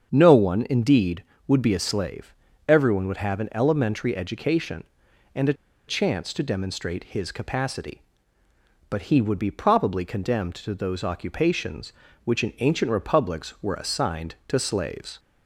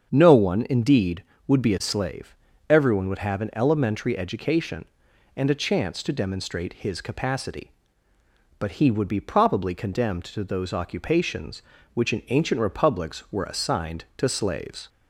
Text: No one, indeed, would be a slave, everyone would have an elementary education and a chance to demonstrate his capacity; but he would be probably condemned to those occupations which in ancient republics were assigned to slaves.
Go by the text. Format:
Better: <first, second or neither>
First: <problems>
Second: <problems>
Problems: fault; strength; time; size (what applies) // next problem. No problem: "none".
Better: second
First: starts louder than the rest; strong; until 1.1 s; 7 dB // pauses between "a" and "chance"; slight; at 5.5 s; 0.34 s long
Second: starts louder than the rest; strong; until 1.1 s; 7 dB